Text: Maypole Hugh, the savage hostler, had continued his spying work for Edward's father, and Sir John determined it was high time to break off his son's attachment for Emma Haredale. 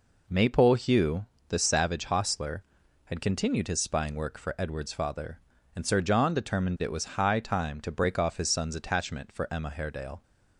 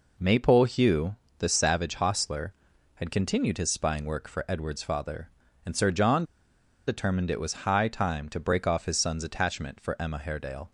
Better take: first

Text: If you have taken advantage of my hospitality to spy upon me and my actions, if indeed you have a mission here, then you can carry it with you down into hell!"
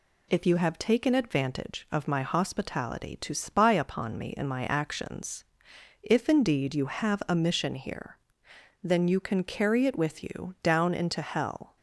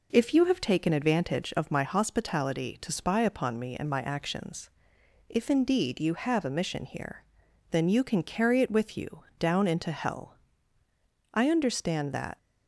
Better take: first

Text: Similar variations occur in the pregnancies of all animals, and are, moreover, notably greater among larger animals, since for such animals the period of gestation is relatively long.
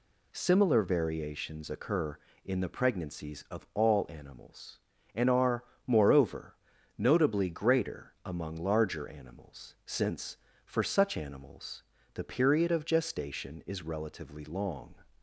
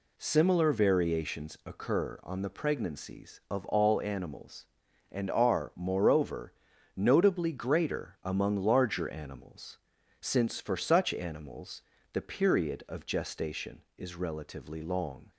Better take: first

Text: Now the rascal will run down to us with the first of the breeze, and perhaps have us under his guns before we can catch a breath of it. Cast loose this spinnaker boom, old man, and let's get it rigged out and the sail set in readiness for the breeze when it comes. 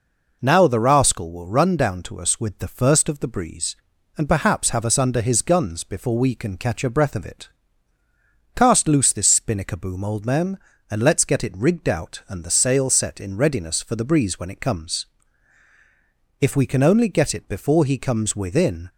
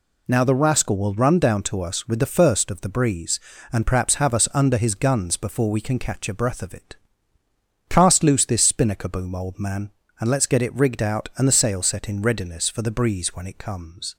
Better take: second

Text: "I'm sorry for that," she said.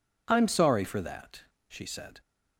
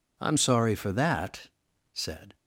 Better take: first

